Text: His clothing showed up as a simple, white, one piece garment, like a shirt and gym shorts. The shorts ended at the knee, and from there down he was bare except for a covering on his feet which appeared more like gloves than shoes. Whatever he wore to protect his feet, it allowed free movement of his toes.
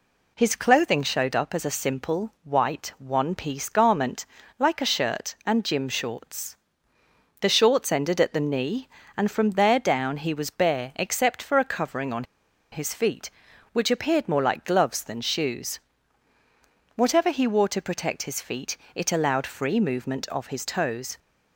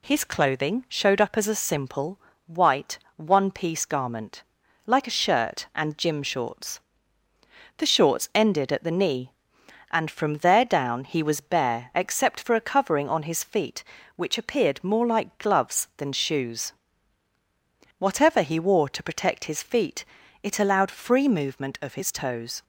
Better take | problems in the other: second | pauses between "on" and "his"; noticeable; at 12.2 s; 0.48 s long

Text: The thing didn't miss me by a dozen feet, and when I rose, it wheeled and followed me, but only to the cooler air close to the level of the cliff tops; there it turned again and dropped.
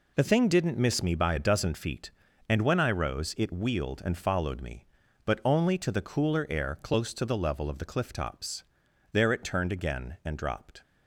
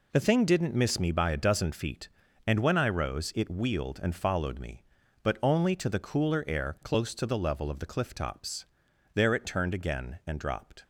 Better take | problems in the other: neither | none

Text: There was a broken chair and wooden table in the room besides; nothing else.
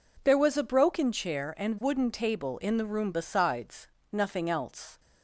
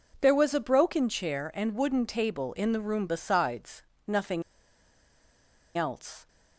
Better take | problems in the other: first | pauses between "nothing" and "else"; strong; at 4.4 s; 1.3 s long

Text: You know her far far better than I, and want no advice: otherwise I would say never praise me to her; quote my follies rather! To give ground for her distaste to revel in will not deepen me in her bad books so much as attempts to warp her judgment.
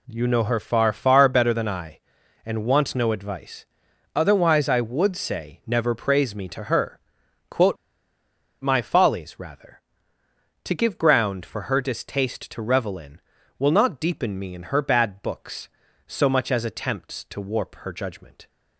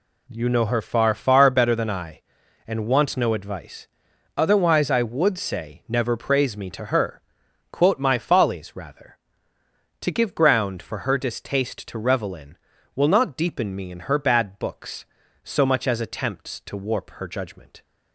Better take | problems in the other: second | pauses between "quote" and "my"; noticeable; at 7.7 s; 0.85 s long

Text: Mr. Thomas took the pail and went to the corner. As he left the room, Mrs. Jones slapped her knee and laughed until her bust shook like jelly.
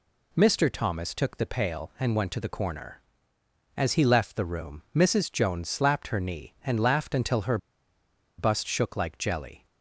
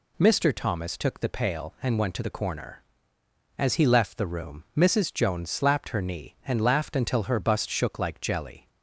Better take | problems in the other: second | pauses between "her" and "bust"; noticeable; at 7.5 s; 0.80 s long

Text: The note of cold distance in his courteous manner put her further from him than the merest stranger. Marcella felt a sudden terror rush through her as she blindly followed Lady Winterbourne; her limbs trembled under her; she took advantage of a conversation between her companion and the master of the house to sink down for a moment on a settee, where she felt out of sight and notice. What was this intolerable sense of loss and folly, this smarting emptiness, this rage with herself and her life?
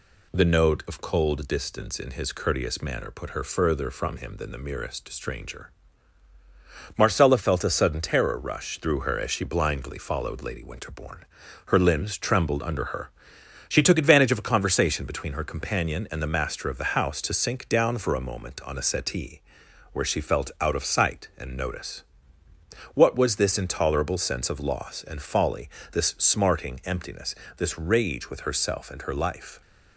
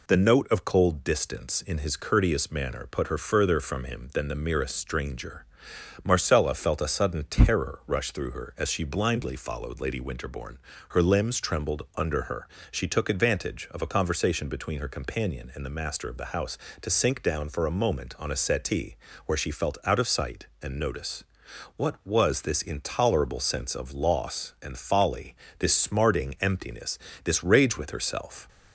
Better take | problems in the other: first | stops before "and her life"; at 28.4 s

